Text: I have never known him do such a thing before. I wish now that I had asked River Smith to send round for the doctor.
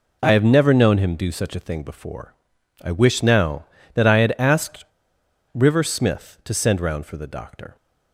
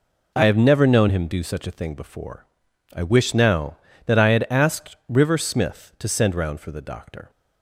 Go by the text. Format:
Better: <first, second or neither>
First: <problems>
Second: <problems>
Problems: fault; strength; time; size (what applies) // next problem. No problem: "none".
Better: second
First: pauses between "asked" and "River"; noticeable; at 4.8 s; 0.70 s long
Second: none